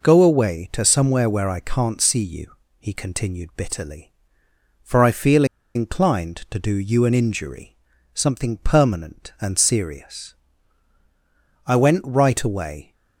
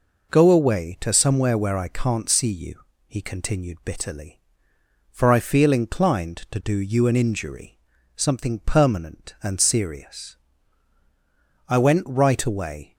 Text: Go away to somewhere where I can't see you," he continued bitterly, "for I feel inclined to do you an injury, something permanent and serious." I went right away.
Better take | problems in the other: second | pauses between "feel" and "inclined"; slight; at 5.4 s; 0.30 s long

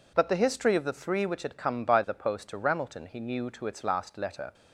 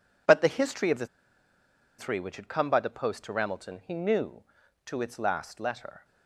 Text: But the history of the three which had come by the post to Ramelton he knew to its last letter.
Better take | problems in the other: first | pauses between "the" and "three"; noticeable; at 1.0 s; 0.92 s long

